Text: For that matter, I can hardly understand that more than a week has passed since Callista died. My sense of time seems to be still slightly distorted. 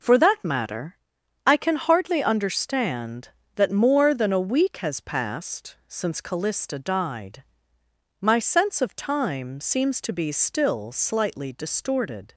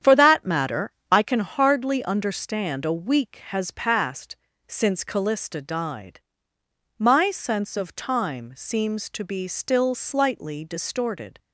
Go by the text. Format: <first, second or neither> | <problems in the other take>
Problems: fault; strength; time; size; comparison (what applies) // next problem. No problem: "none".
first | starts louder than the rest; strong; until 1.2 s; 9 dB // skips "that more than"; at 2.8 s // pauses between "passed" and "since"; slight; at 4.3 s; 0.32 s long